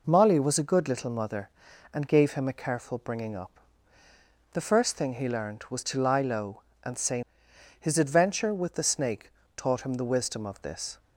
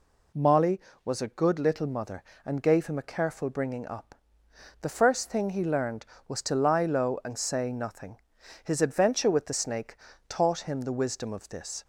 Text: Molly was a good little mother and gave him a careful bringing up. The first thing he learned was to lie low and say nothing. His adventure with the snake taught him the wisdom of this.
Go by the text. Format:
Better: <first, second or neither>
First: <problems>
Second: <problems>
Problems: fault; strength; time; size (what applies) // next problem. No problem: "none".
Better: second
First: skips "nothing"; at 7.5 s // pauses between "snake" and "taught"; slight; at 9.3 s; 0.26 s long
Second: pauses between "snake" and "taught"; slight; at 9.9 s; 0.32 s long